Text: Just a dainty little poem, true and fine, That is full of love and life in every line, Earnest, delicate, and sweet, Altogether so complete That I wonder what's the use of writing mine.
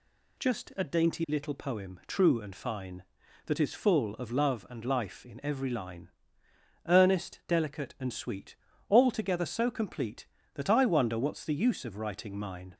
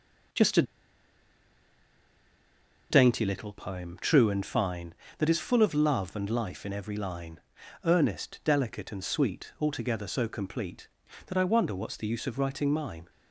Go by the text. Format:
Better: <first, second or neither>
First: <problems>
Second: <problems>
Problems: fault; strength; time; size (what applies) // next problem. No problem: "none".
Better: first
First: none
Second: pauses between "a" and "dainty"; strong; at 0.6 s; 2.2 s long